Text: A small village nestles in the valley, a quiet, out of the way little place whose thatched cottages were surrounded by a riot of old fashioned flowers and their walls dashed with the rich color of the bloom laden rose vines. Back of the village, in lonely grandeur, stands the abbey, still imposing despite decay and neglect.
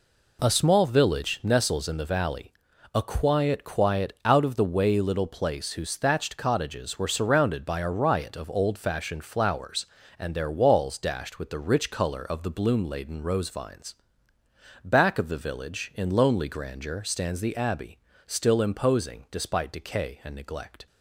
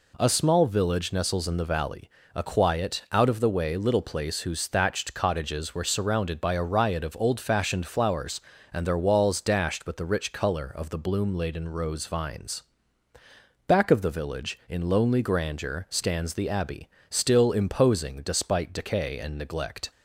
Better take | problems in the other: second | says "quiet" twice; at 3.6 s

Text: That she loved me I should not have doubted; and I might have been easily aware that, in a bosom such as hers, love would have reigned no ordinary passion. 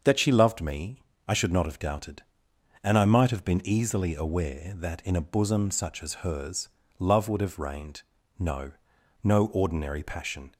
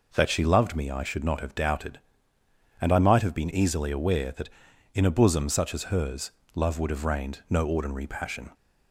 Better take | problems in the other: second | starts louder than the rest; until 1.3 s; 6.5 dB // pauses between "me" and "I"; slight; at 1.0 s; 0.26 s long // pauses between "reigned" and "no"; at 8.0 s; 0.38 s long // says "no" twice; at 9.2 s

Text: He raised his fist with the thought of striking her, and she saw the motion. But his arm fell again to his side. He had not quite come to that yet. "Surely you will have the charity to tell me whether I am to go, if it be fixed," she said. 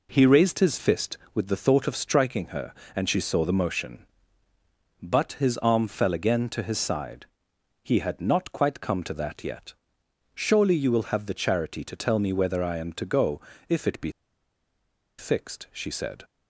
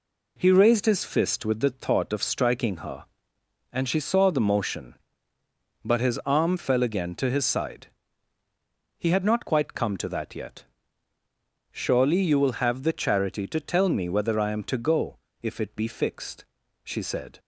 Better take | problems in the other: second | pauses between "be" and "fixed"; at 14.1 s; 1.0 s long

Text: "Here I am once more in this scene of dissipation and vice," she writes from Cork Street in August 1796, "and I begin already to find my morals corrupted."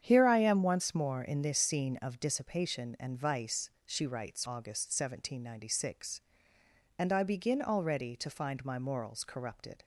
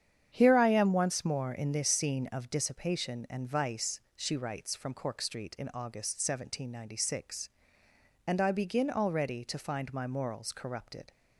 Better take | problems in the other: second | starts louder than the rest; strong; until 1.0 s; 8.5 dB; strong in the second // skips "from Cork Street in"; at 4.4 s

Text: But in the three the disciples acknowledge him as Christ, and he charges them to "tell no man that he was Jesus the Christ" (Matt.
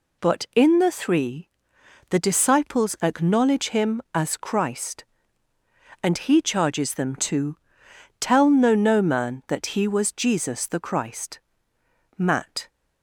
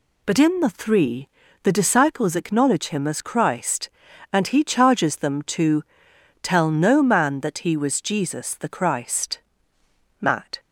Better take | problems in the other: second | pauses between "three" and "the"; noticeable; at 1.4 s; 0.62 s long; slight in the second // pauses between "to" and "tell"; noticeable; at 7.5 s; 0.62 s long; noticeable in the second // says "no" twice; at 8.7 s

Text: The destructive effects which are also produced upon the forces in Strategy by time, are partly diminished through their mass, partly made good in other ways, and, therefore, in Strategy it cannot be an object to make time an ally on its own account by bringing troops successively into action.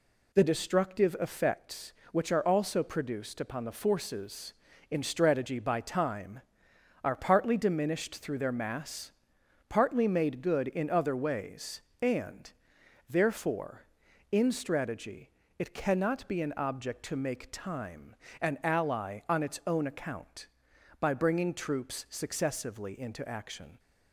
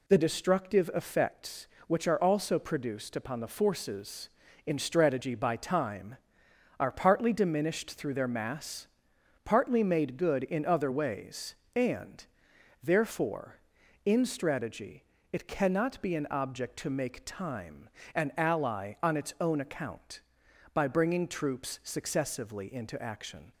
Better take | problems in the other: neither | pauses between "Strategy" and "it"; slight; the same in both // pauses between "time" and "an"; slight; the same in both

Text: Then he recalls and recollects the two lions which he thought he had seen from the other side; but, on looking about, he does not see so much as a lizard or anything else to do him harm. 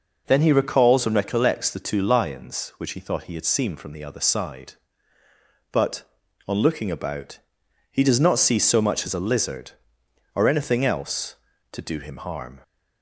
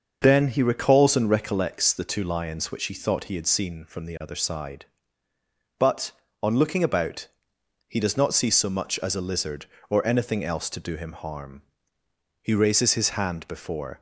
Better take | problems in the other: first | starts louder than the rest; until 1.2 s; 6.5 dB // goes on to say "He raises his hand before"; from 12.4 s on; 1.5 s long

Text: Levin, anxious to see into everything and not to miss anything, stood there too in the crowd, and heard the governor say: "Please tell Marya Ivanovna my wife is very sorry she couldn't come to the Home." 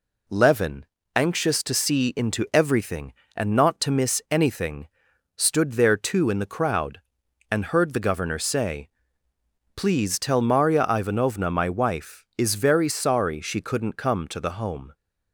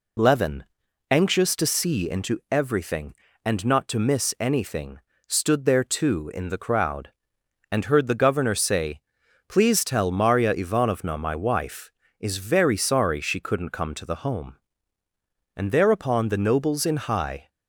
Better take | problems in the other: first | goes on to say "And thereupon the nobles in high"; strong; from 15.5 s on; 1.9 s long

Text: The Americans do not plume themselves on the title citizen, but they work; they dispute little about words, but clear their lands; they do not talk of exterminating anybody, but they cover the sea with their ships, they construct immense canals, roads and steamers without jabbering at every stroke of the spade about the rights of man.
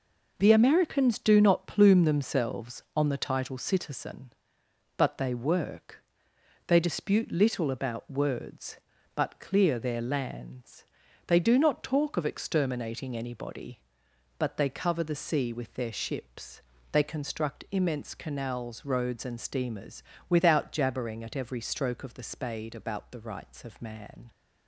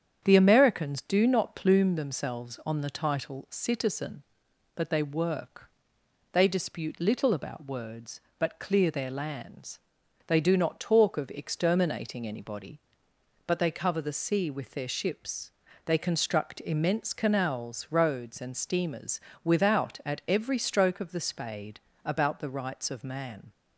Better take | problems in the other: first | starts louder than the rest; strong; until 1.2 s; 8.5 dB // pauses between "steamers" and "without"; slight; at 19.1 s; 0.24 s long; slight in the first // skips "jabbering"; at 20.0 s // pauses between "spade" and "about"; slight; at 21.8 s; 0.24 s long

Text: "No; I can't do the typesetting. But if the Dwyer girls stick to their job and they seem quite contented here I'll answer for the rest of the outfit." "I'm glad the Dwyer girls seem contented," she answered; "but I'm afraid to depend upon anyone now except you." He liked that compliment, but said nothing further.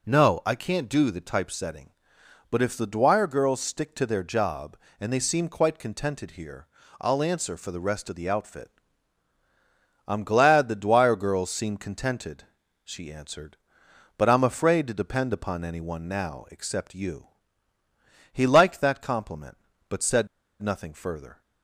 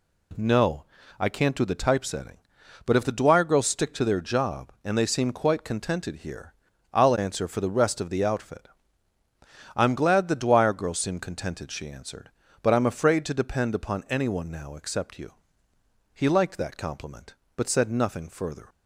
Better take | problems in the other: second | pauses between "here" and "I'll"; slight; at 6.6 s; 0.34 s long; also in the second // pauses between "said" and "nothing"; slight; at 20.2 s; 0.33 s long

